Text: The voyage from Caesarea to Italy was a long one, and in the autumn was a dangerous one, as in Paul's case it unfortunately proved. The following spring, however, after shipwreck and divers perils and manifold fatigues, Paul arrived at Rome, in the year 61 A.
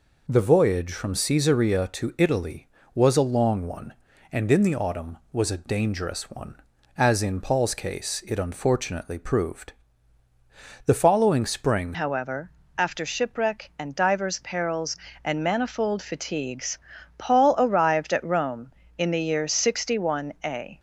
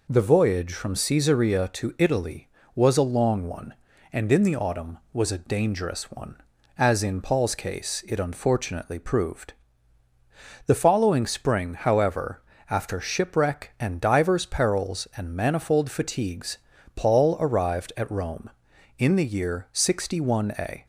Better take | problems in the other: second | changes voice at "however"; from 11.9 s on; 8.8 s long

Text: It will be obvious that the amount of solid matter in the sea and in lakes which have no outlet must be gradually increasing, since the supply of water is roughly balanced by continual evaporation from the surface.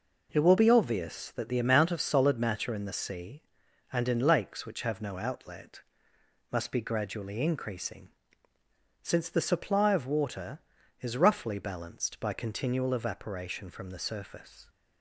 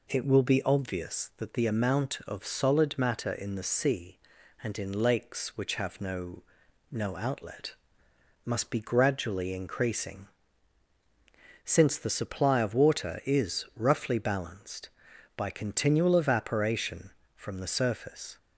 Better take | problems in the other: first | says "no" twice; at 6.8 s // pauses between "outlet" and "must"; noticeable; at 7.7 s; 0.70 s long; noticeable in the first

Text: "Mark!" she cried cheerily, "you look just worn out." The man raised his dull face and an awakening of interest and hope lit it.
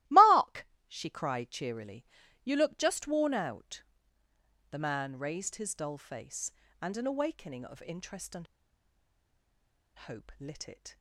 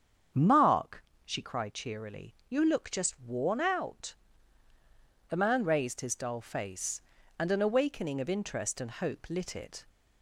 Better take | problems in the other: second | starts louder than the rest; strong; until 1.2 s; 17 dB; strong in the second // pauses between "and" and "hope"; strong; at 8.4 s; 1.5 s long

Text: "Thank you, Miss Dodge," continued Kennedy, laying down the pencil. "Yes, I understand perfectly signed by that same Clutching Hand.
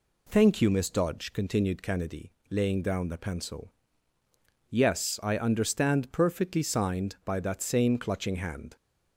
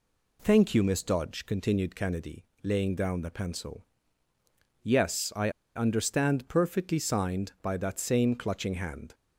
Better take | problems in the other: first | pauses between "I" and "understand"; slight; at 5.5 s; 0.25 s long

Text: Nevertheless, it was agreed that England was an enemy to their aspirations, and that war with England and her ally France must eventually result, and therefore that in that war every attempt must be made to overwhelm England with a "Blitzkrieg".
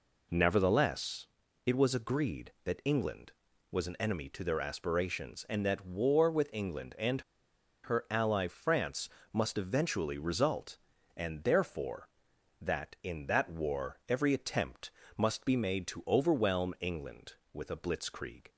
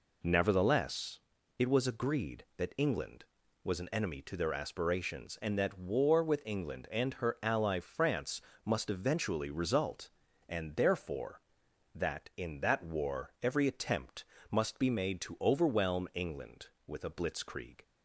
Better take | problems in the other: second | pauses between "and" and "her"; noticeable; at 7.2 s; 0.63 s long // pauses between "France" and "must"; slight; at 9.0 s; 0.24 s long; slight in the second // pauses between "attempt" and "must"; slight; at 14.9 s; 0.26 s long; slight in the second

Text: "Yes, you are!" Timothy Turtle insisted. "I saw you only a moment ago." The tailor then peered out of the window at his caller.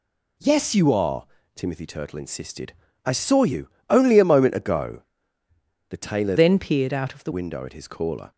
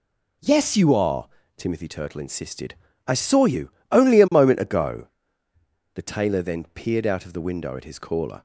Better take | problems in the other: second | pauses between "you" and "only"; slight; at 3.6 s; 0.20 s long; slight in the second // changes voice from "then" to "the"; from 6.3 to 7.3 s; 1.0 s long

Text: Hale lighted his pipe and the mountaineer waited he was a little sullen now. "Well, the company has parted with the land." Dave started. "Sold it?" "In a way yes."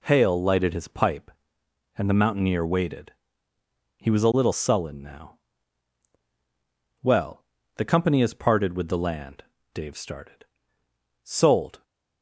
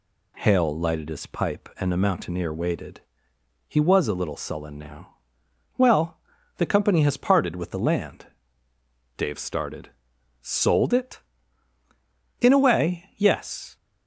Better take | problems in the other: second | pauses between "waited" and "he"; noticeable; at 3.1 s; 0.86 s long; noticeable in the second // stops before "it In a way yes"; at 11.8 s

